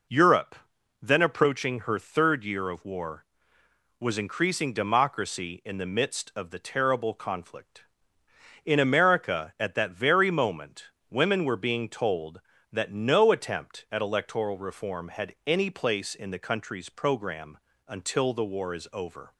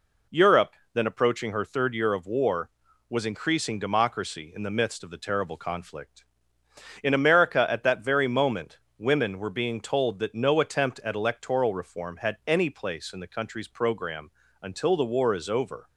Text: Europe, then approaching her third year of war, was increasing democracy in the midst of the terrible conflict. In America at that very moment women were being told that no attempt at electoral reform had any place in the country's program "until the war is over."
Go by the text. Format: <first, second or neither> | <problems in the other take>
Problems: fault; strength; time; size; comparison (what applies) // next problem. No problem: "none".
neither | pauses between "moment" and "women"; slight; the same in both // pauses between "program" and "until"; slight; the same in both